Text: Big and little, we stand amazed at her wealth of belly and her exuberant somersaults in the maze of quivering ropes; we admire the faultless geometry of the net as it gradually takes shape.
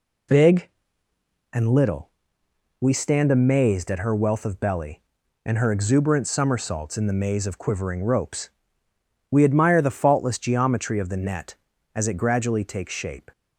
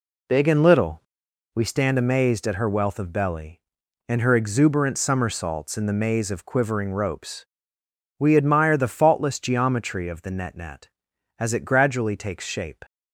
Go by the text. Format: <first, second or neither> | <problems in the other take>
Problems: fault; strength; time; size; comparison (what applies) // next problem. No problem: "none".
first | says "net" twice; at 10.5 s